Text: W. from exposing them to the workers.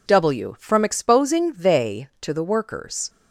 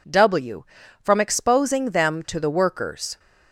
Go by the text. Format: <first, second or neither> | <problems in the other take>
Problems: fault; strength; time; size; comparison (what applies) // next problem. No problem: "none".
second | says "they" for "them"; at 1.5 s